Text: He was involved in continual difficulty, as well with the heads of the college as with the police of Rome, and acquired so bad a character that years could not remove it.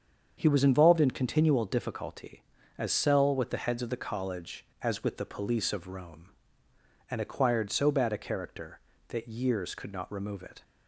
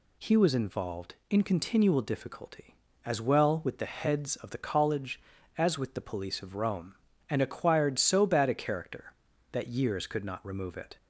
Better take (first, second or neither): second